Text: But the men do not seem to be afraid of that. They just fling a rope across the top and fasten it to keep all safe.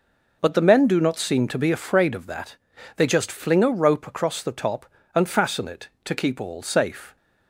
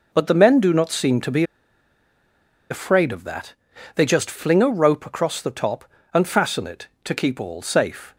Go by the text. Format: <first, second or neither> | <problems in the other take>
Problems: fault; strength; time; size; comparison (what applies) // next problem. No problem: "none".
first | pauses between "be" and "afraid"; strong; at 1.4 s; 1.2 s long